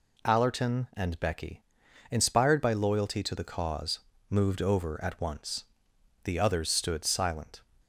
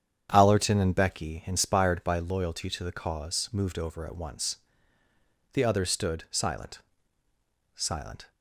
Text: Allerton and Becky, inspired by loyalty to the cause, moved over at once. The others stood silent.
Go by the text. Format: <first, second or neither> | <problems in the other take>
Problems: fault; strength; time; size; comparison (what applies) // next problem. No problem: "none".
first | starts louder than the rest; strong; until 1.3 s; 8.5 dB // says "silent" twice; at 7.7 s